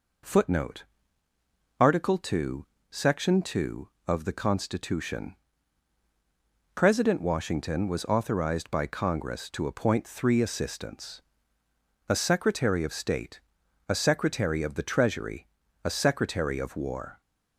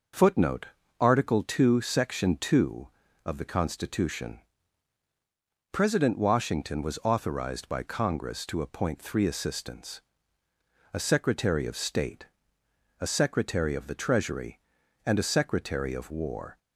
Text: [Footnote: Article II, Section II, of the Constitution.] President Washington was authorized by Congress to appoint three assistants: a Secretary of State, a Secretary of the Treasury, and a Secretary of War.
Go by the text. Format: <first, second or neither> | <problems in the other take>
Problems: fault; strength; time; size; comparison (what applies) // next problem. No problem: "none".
second | skips "and"; at 15.6 s